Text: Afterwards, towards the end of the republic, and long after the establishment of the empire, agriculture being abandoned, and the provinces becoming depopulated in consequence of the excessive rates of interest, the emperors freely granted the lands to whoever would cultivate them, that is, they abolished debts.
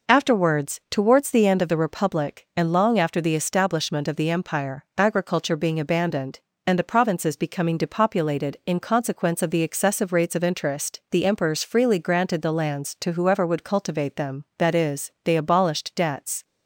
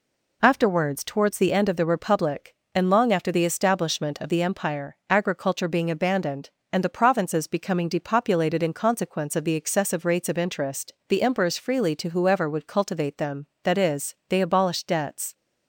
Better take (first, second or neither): first